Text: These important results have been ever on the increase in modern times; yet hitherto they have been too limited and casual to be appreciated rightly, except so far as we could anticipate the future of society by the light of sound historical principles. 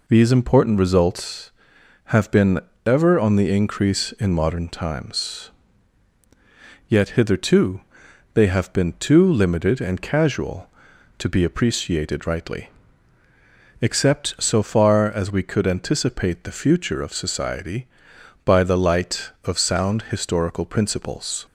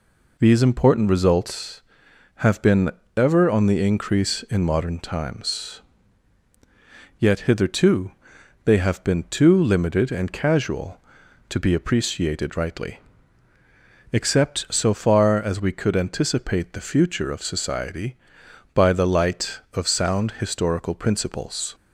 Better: neither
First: pauses between "been" and "ever"; slight; at 2.5 s; 0.26 s long // pauses between "hitherto" and "they"; noticeable; at 7.8 s; 0.54 s long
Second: pauses between "been" and "ever"; slight; at 2.8 s; 0.26 s long // pauses between "hitherto" and "they"; noticeable; at 8.1 s; 0.54 s long

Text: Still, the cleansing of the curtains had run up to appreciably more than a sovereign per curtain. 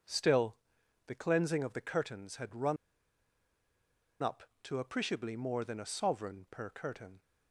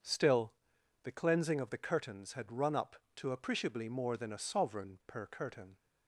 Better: second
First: pauses between "run" and "up"; strong; at 2.7 s; 1.4 s long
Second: none

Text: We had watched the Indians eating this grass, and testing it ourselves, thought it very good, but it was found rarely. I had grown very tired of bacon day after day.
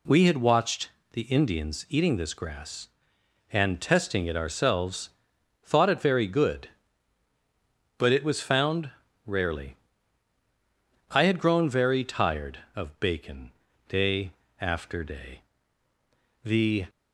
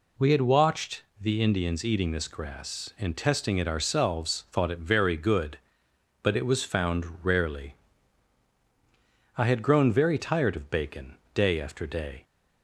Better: second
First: pauses between "watched" and "the"; slight; at 0.9 s; 0.24 s long // pauses between "found" and "rarely"; slight; at 8.9 s; 0.36 s long // pauses between "bacon" and "day"; at 13.5 s; 0.40 s long // pauses between "day" and "after"; slight; at 14.3 s; 0.28 s long // goes on to say "The"; slight; from 16.4 s on; 0.42 s long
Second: pauses between "watched" and "the"; slight; at 1.0 s; 0.18 s long // pauses between "found" and "rarely"; slight; at 7.0 s; 0.16 s long // pauses between "bacon" and "day"; slight; at 11.1 s; 0.20 s long

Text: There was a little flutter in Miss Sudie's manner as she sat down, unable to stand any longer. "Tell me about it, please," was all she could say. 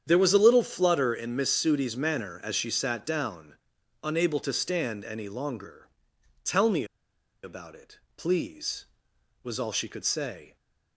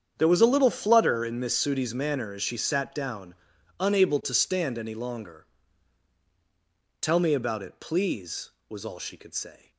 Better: second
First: starts louder than the rest; strong; until 1.0 s; 8.5 dB // pauses between "me" and "about"; noticeable; at 6.8 s; 0.58 s long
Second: starts louder than the rest; strong; until 1.1 s; 8 dB

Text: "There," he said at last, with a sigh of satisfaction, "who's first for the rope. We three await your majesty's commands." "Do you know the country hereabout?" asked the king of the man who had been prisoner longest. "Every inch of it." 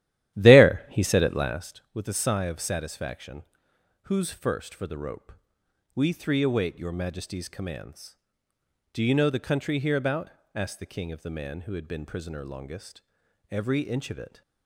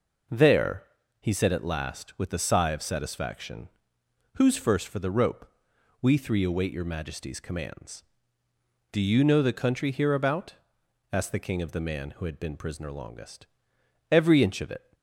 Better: second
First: starts louder than the rest; strong; until 1.7 s; 13 dB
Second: none

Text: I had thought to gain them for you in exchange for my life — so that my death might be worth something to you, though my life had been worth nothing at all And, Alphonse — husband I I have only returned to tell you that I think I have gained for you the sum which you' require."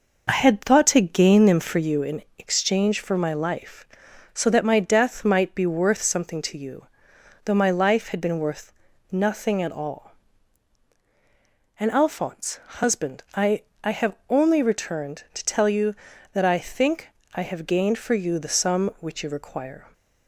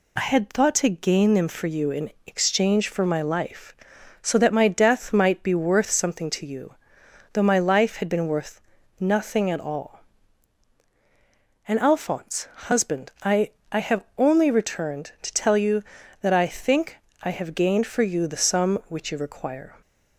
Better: second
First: starts louder than the rest; noticeable; until 2.1 s; 5 dB // pauses between "in" and "exchange"; slight; at 2.2 s; 0.16 s long // pauses between "worth" and "nothing"; at 8.7 s; 0.40 s long // pauses between "I" and "I"; slight; at 13.6 s; 0.20 s long // pauses between "think" and "I"; slight; at 17.0 s; 0.24 s long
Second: pauses between "in" and "exchange"; slight; at 2.0 s; 0.16 s long // pauses between "worth" and "nothing"; at 8.5 s; 0.40 s long // pauses between "I" and "I"; slight; at 13.5 s; 0.20 s long // pauses between "think" and "I"; slight; at 16.9 s; 0.24 s long

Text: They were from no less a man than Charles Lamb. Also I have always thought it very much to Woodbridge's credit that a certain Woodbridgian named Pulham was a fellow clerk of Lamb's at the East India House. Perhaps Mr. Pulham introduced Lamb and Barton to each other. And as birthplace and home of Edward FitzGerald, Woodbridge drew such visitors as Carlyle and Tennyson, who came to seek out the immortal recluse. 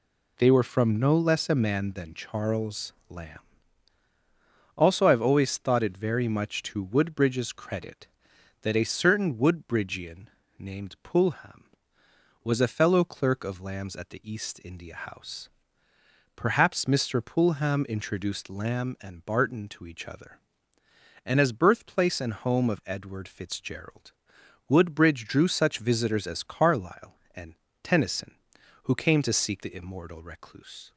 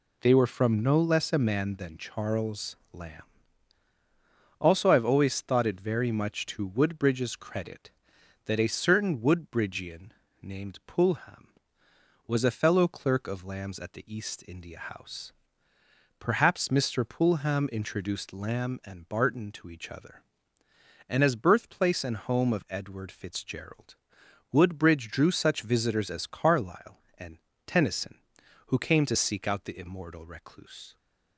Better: second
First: pauses between "Charles" and "Lamb"; slight; at 2.9 s; 0.16 s long // pauses between "Woodbridgian" and "named"; slight; at 10.2 s; 0.30 s long // pauses between "and" and "Tennyson"; slight; at 27.5 s; 0.28 s long // skips "out"; at 29.6 s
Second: pauses between "Charles" and "Lamb"; slight; at 2.7 s; 0.16 s long // pauses between "Woodbridgian" and "named"; slight; at 10.1 s; 0.30 s long // pauses between "and" and "Tennyson"; slight; at 27.3 s; 0.28 s long

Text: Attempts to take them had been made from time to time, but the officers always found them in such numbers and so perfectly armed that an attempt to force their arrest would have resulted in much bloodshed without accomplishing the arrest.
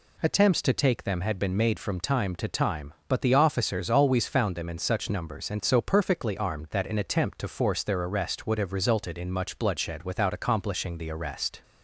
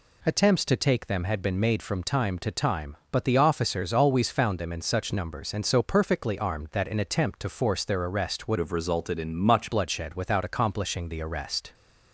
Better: first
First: none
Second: changes voice from "have" to "much"; from 8.5 to 9.7 s; 1.2 s long

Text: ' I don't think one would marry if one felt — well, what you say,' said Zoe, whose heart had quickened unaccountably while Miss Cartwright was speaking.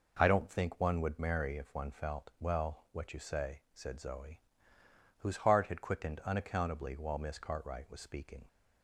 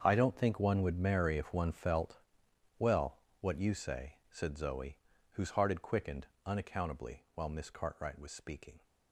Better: first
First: none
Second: gets quieter; strong; throughout; 14.5 dB // pauses between "quickened" and "unaccountably"; slight; at 6.2 s; 0.18 s long

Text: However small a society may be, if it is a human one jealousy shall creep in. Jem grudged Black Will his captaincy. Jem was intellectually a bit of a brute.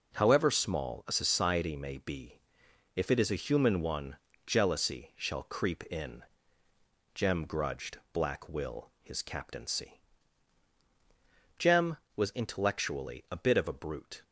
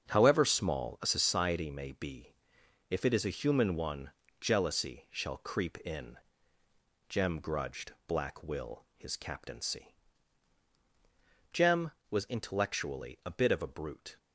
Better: first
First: pauses between "one" and "jealousy"; slight; at 4.1 s; 0.28 s long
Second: starts louder than the rest; until 1.3 s; 7 dB // pauses between "one" and "jealousy"; slight; at 4.1 s; 0.28 s long

